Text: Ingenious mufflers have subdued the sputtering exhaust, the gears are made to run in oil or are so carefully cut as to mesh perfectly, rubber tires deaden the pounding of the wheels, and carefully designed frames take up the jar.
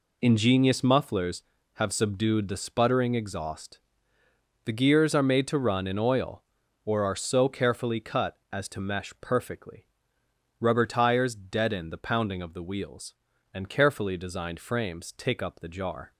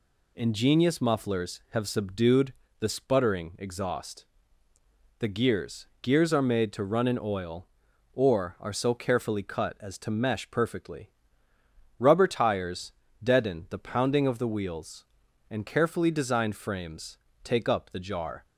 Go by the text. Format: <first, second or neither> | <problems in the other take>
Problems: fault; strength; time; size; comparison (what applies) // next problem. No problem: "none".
first | pauses between "subdued" and "the"; slight; at 2.5 s; 0.26 s long // says "gears" twice; at 6.0 s // pauses between "tires" and "deaden"; slight; at 12.9 s; 0.28 s long // pauses between "frames" and "take"; slight; at 17.1 s; 0.26 s long